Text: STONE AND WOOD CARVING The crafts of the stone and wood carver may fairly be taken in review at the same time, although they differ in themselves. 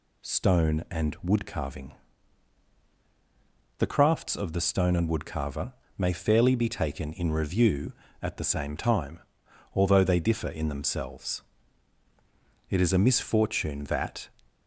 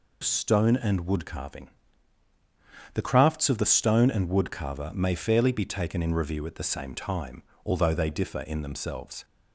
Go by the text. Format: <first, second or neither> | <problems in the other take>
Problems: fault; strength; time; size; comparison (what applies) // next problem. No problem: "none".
second | pauses between "CARVING" and "The"; strong; at 1.9 s; 1.8 s long; strong in the second // pauses between "carver" and "may"; slight; at 5.7 s; 0.26 s long // goes on to say "It is a misfortune that"; from 12.6 s on; 1.6 s long